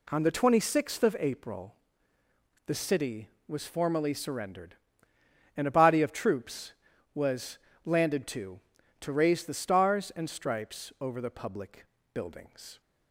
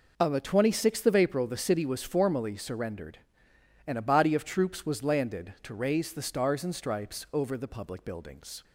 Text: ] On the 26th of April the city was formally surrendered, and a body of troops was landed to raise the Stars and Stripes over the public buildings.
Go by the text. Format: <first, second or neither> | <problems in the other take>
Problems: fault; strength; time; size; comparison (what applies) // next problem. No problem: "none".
second | pauses between "April" and "the"; noticeable; at 1.7 s; 0.90 s long // pauses between "was" and "landed"; slight; at 7.5 s; 0.26 s long // says "to" twice; at 9.0 s // pauses between "public" and "buildings"; slight; at 11.8 s; 0.28 s long